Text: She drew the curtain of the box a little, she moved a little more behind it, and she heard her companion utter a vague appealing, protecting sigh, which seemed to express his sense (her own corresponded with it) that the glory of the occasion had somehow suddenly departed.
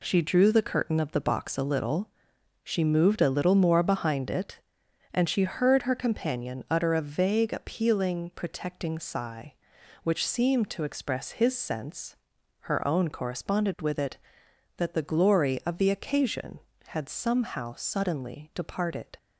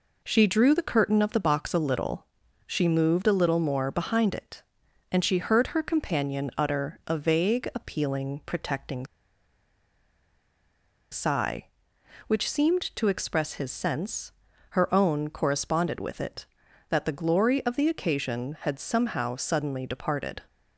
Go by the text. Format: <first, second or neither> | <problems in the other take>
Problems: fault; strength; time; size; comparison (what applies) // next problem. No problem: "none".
first | pauses between "protecting" and "sigh"; strong; at 9.0 s; 2.0 s long